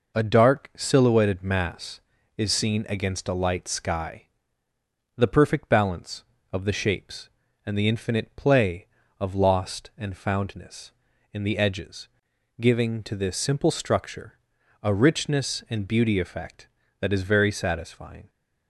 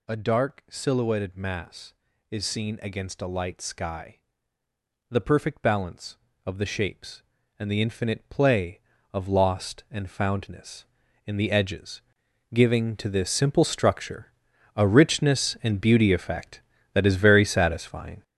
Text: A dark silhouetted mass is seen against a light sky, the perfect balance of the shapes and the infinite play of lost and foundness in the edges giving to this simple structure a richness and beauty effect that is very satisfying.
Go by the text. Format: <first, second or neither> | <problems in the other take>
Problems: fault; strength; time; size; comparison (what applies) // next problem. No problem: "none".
first | gets louder; strong; throughout; 8 dB // pauses between "edges" and "giving"; noticeable; at 12.0 s; 0.52 s long; noticeable in the first // pauses between "structure" and "a"; at 14.3 s; 0.42 s long; also in the first